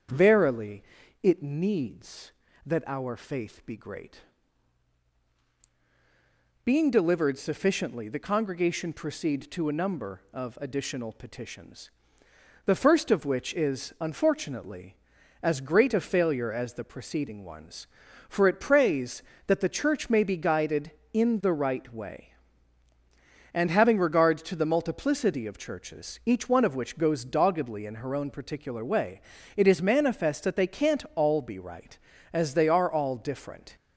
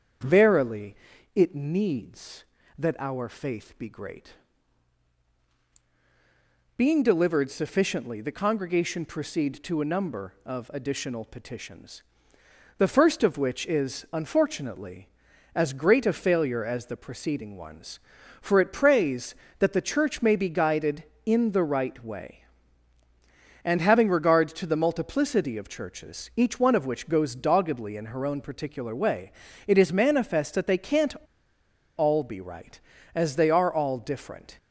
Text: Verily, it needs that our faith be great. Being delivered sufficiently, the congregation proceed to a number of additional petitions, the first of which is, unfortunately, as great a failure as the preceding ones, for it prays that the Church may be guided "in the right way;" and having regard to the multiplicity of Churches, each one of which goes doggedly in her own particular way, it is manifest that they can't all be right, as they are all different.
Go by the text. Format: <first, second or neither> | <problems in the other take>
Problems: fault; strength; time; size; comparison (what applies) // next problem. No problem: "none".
first | starts louder than the rest; strong; until 1.6 s; 7 dB; strong in the first // pauses between "can't" and "all"; noticeable; at 31.1 s; 0.83 s long